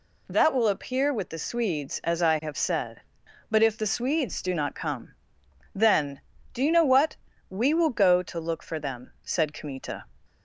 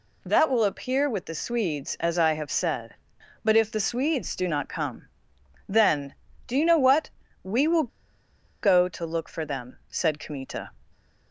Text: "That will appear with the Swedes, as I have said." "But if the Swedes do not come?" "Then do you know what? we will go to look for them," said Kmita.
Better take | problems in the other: first | pauses between "will" and "go"; noticeable; at 7.8 s; 0.73 s long

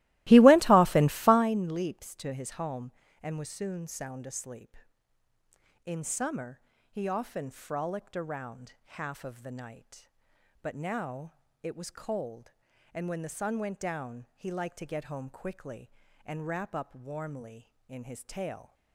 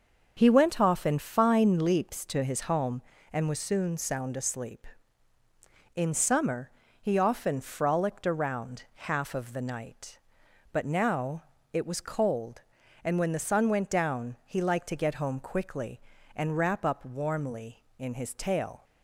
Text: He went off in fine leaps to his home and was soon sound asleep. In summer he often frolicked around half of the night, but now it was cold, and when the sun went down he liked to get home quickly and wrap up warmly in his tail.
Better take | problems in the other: second | starts louder than the rest; strong; until 1.5 s; 17.5 dB // pauses between "summer" and "he"; slight; at 6.5 s; 0.32 s long; slight in the second // pauses between "around" and "half"; slight; at 8.7 s; 0.24 s long; slight in the second // pauses between "now" and "it"; slight; at 11.3 s; 0.32 s long; slight in the second

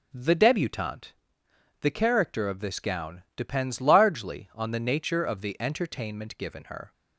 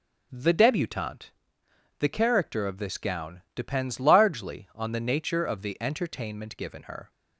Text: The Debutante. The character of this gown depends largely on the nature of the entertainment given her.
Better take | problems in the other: neither | none

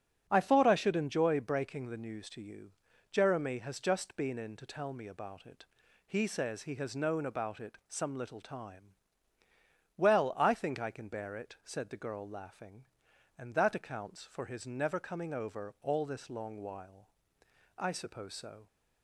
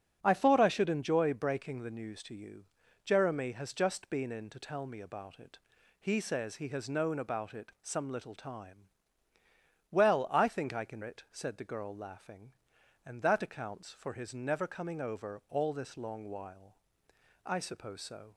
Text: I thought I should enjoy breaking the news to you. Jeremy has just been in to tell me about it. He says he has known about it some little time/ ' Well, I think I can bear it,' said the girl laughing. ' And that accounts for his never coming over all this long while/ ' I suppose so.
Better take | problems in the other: first | starts louder than the rest; strong; until 1.2 s; 11.5 dB; strong in the first // skips "bear"; at 11.0 s

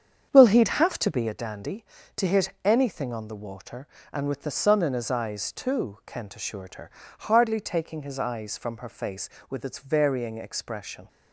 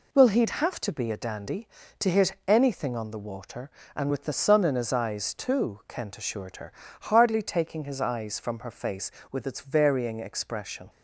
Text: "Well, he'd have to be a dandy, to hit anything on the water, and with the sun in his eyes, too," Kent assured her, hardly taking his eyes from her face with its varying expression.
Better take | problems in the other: second | starts louder than the rest; strong; until 1.4 s; 7.5 dB

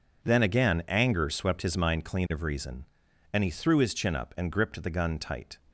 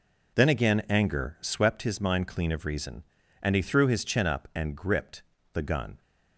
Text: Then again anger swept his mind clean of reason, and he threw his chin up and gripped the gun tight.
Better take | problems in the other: first | pauses between "gripped" and "the"; slight; at 5.2 s; 0.32 s long // stops before "tight"; at 6.0 s

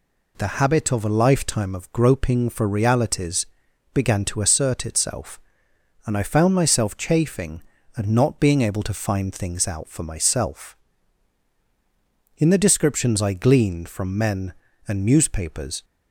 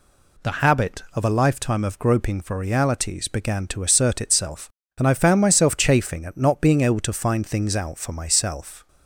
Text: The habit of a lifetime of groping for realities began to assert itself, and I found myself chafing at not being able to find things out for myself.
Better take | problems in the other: second | pauses between "realities" and "began"; noticeable; at 3.4 s; 0.48 s long // goes on to say "In the descriptions I gleaned from men and newspapers"; strong; from 12.3 s on; 3.4 s long

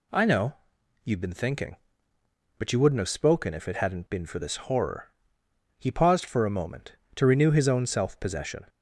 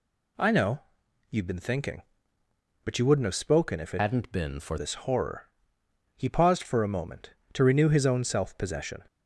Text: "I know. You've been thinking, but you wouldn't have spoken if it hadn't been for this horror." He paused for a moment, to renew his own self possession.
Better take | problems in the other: first | changes voice from "hadn't" to "for"; from 3.9 to 4.7 s; 0.8 s long

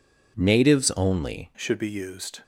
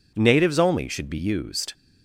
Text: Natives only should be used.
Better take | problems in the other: second | changes voice at "should"; from 1.5 s on; 0.9 s long

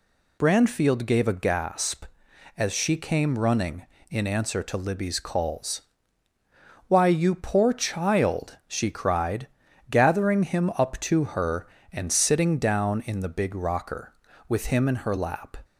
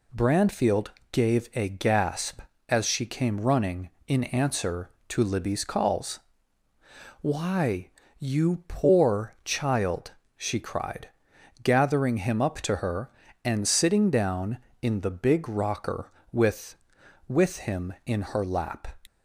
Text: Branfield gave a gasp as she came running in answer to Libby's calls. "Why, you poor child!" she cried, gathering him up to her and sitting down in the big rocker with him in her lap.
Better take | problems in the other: first | pauses between "Branfield" and "gave"; slight; at 0.8 s; 0.24 s long // says "with" twice; at 17.2 s

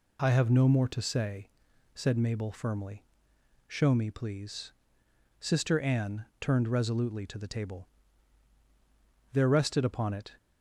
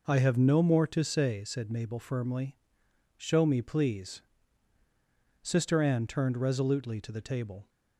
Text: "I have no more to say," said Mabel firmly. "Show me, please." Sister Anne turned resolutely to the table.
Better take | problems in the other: second | goes on to say "There rested upon it"; noticeable; from 9.3 s on; 1.0 s long

